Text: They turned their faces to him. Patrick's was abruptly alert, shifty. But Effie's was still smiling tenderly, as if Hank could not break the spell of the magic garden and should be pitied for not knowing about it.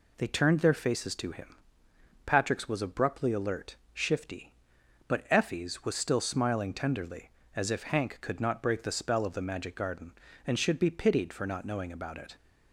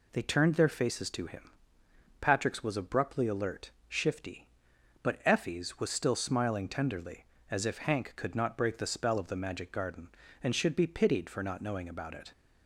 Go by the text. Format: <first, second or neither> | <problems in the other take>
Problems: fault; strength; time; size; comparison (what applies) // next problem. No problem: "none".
neither | none